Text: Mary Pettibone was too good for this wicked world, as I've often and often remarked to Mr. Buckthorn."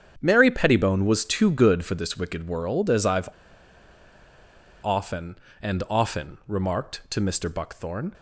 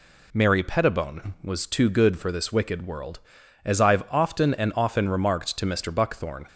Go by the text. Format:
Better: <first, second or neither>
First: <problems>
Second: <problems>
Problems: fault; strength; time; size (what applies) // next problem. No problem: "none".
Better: second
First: starts louder than the rest; strong; until 1.1 s; 8.5 dB // pauses between "I've" and "often"; strong; at 3.2 s; 1.5 s long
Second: none